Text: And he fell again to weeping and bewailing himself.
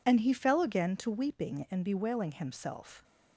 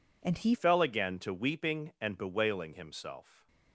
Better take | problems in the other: first | changes voice at "fell"; from 0.5 s on; 2.9 s long // stays silent after the last word; slight; from 3.2 s on; 0.5 s long

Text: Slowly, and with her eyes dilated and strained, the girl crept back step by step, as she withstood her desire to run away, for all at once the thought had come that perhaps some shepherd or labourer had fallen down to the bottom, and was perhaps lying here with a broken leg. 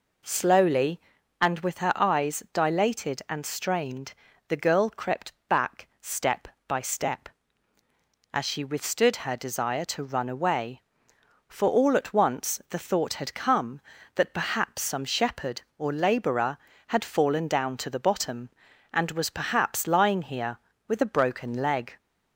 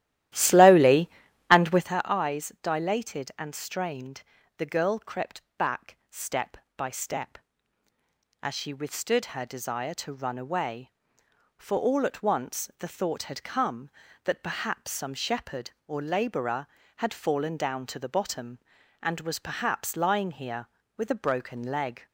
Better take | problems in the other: first | starts louder than the rest; strong; until 2.0 s; 13.5 dB // pauses between "crept" and "back"; slight; at 5.4 s; 0.16 s long; slight in the first

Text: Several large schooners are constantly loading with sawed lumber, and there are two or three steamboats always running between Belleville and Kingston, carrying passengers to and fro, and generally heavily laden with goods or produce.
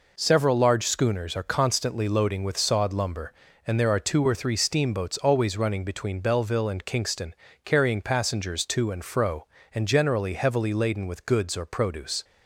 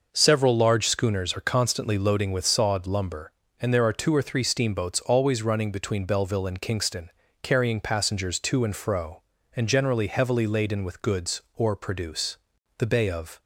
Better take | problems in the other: first | goes on to say "The Bay of"; noticeable; from 12.7 s on; 0.62 s long

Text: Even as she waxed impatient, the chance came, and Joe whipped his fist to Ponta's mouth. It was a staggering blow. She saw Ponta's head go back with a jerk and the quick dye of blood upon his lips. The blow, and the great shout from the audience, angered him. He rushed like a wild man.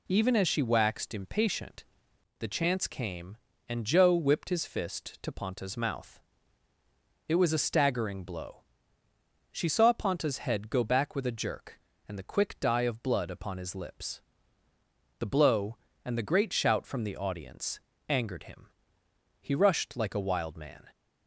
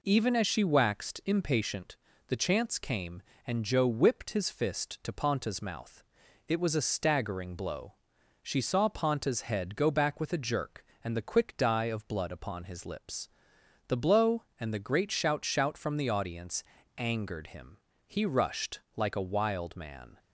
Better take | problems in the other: first | says "shout" twice; at 15.4 s // pauses between "rushed" and "like"; slight; at 18.7 s; 0.16 s long

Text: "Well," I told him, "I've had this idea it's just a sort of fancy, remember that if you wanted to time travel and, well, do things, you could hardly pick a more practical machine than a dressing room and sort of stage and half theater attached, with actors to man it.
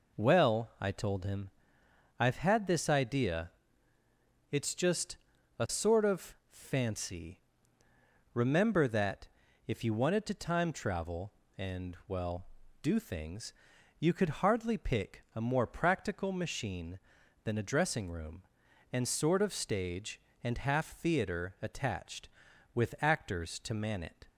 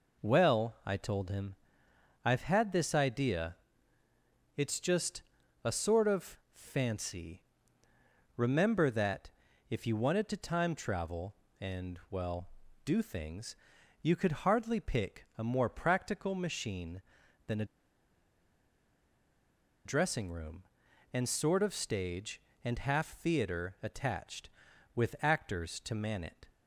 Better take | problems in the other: first | pauses between "idea" and "it's"; at 3.5 s; 1.0 s long; also in the first // pauses between "just" and "a"; at 5.2 s; 0.40 s long; also in the first // pauses between "of" and "fancy"; slight; at 6.3 s; 0.16 s long; slight in the first // pauses between "that" and "if"; at 9.3 s; 0.38 s long; also in the first // pauses between "a" and "dressing"; strong; at 17.6 s; 2.2 s long

